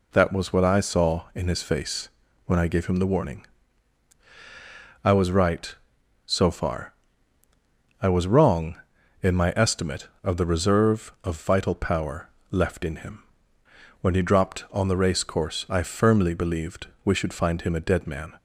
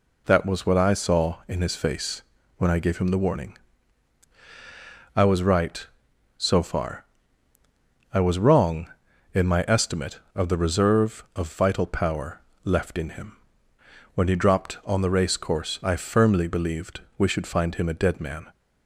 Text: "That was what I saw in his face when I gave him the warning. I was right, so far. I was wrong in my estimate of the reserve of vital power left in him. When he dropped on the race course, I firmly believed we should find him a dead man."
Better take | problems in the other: neither | pauses between "face" and "when"; the same in both // pauses between "power" and "left"; slight; the same in both // pauses between "believed" and "we"; slight; the same in both

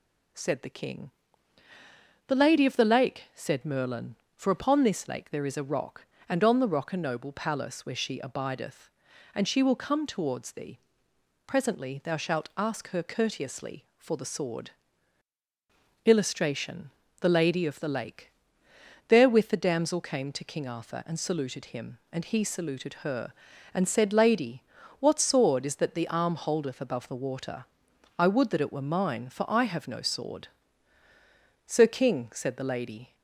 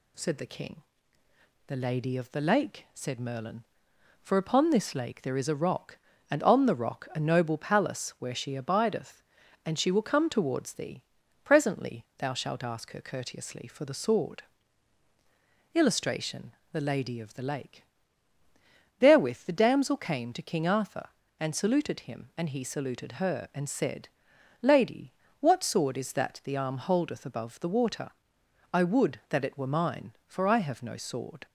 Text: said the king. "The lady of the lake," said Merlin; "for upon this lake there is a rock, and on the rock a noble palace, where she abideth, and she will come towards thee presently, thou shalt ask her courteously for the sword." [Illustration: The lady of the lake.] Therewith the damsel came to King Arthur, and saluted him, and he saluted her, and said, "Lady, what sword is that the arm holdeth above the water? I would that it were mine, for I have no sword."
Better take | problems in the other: second | pauses between "thee" and "presently"; noticeable; at 10.7 s; 0.66 s long; also in the second // goes on to say "Sir King said the lady"; from 31.6 s on; 1.4 s long

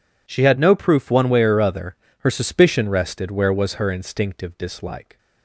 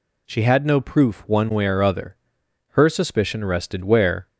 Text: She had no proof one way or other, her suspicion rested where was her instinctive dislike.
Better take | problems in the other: first | stops before "was her instinctive dislike"; at 4.2 s

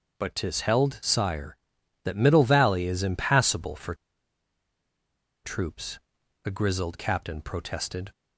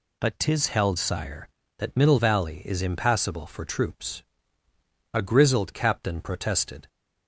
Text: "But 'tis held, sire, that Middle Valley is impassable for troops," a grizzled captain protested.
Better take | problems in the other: second | starts louder than the rest; noticeable; until 1.2 s; 6 dB // pauses between "for" and "troops"; strong; at 3.9 s; 1.5 s long

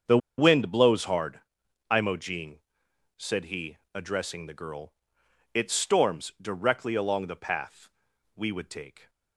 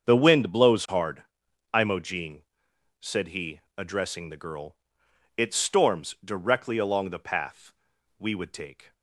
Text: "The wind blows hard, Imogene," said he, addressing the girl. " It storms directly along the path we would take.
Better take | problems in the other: second | starts louder than the rest; strong; until 1.2 s; 7 dB; strong in the second // pauses between "The" and "wind"; slight; at 0.1 s; 0.20 s long // pauses between "path" and "we"; at 7.8 s; 0.44 s long; also in the second

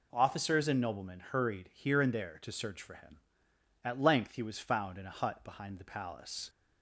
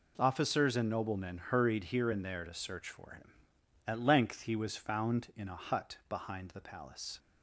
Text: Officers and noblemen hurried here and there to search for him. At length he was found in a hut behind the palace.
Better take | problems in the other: neither | none

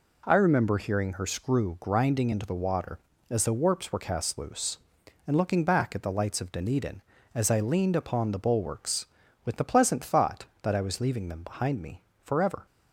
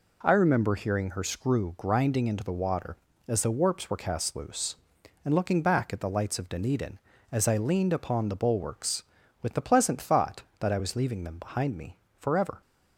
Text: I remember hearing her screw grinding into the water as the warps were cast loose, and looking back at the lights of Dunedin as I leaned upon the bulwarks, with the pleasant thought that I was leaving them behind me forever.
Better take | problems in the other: neither | pauses between "me" and "forever"; slight; the same in both

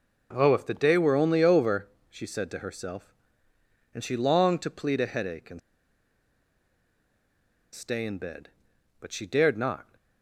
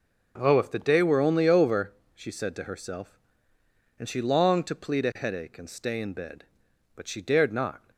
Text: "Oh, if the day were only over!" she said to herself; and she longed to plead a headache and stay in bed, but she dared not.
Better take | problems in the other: second | pauses between "and" and "stay"; strong; at 5.5 s; 2.1 s long

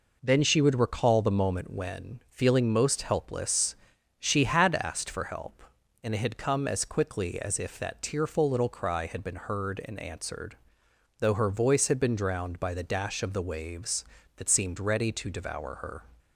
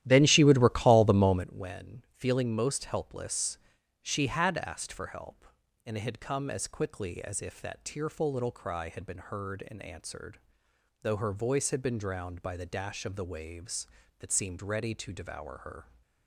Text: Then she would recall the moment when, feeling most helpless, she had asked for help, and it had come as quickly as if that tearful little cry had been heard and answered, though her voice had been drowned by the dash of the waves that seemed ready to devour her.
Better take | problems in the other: first | starts louder than the rest; strong; until 1.5 s; 12.5 dB

